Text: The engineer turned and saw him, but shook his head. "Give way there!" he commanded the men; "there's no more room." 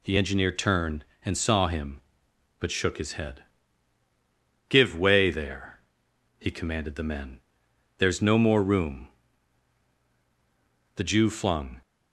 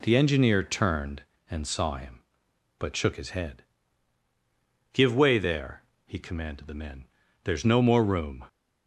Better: second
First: goes on to say "The Jew flung"; noticeable; from 10.9 s on; 0.86 s long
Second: none

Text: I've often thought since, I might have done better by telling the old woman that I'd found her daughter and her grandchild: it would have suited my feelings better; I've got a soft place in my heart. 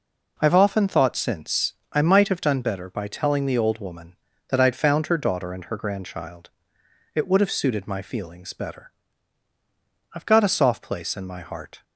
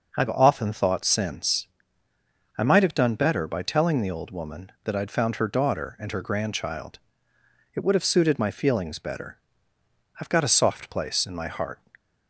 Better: neither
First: none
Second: none

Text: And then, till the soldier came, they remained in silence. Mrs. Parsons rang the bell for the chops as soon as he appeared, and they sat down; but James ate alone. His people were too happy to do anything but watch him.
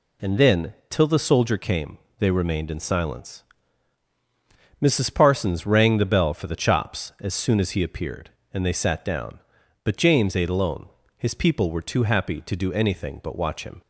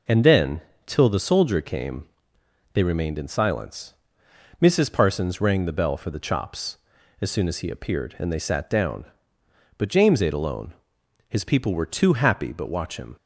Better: first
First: none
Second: skips "to do anything"; at 12.5 s

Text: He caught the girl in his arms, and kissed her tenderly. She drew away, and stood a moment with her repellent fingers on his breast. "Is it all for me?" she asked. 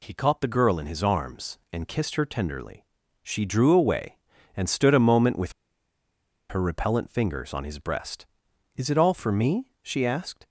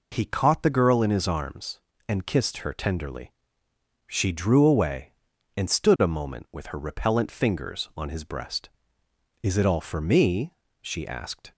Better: second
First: pauses between "with" and "her"; noticeable; at 5.5 s; 0.97 s long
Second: none

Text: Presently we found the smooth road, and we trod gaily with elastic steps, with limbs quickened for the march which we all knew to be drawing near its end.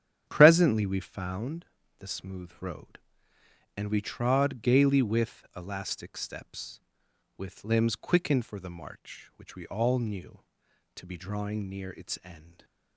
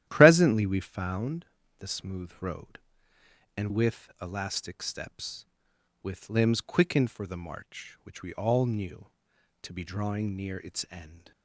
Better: first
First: starts louder than the rest; strong; until 1.2 s; 10.5 dB // pauses between "found" and "the"; slight; at 1.6 s; 0.36 s long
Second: starts louder than the rest; strong; until 1.0 s; 12.5 dB // pauses between "found" and "the"; slight; at 1.4 s; 0.36 s long // skips "we trod gaily"; at 3.6 s

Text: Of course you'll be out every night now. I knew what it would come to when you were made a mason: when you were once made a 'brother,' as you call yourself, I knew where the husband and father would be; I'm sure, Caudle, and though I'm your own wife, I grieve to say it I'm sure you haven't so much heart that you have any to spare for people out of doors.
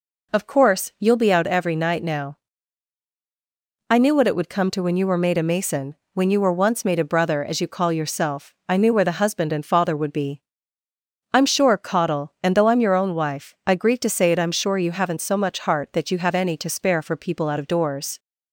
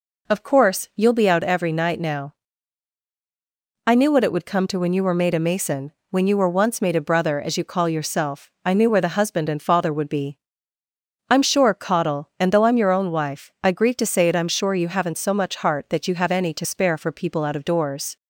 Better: neither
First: none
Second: none

